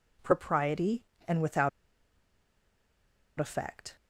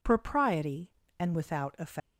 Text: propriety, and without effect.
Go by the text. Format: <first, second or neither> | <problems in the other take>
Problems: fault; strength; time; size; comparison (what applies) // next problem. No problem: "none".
second | pauses between "without" and "effect"; strong; at 1.6 s; 1.6 s long